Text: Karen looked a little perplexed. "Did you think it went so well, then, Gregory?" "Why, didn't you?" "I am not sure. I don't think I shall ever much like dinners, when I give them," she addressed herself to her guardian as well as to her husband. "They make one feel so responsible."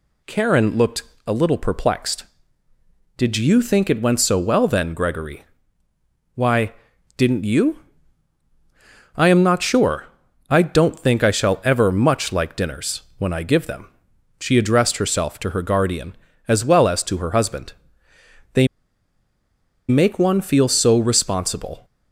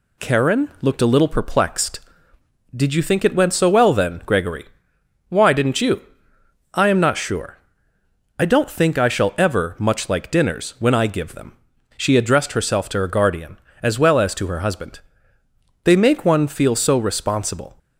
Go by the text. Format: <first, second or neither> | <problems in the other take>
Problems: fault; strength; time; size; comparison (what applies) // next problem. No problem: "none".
second | pauses between "looked" and "a"; slight; at 1.0 s; 0.24 s long // pauses between "They" and "make"; at 18.6 s; 1.2 s long